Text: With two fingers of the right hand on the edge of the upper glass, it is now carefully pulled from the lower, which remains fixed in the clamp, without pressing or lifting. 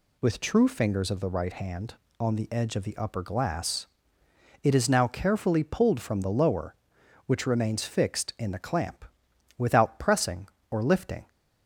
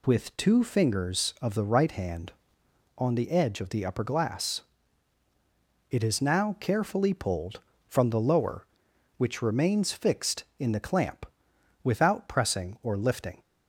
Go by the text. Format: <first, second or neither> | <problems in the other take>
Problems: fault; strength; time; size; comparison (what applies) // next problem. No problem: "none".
second | says "true" for "two"; at 0.3 s